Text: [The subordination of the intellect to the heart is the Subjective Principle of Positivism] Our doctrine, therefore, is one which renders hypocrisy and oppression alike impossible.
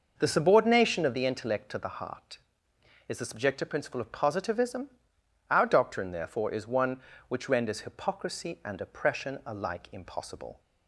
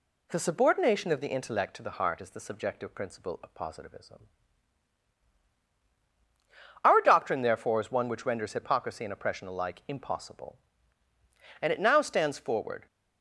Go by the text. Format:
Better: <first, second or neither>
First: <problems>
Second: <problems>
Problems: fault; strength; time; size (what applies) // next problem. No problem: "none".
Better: first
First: pauses between "Positivism" and "Our"; noticeable; at 4.8 s; 0.62 s long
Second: pauses between "Positivism" and "Our"; strong; at 4.2 s; 2.6 s long // goes on to say "And it now stands forward"; noticeable; from 11.6 s on; 1.2 s long